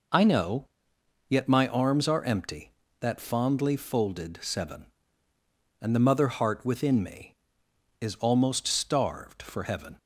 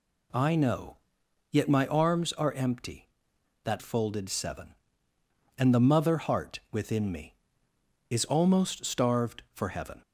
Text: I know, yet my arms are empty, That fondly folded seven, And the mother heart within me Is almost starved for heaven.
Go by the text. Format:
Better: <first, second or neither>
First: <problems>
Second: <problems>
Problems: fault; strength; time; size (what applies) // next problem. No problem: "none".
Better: first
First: none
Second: skips "fondly"; at 3.7 s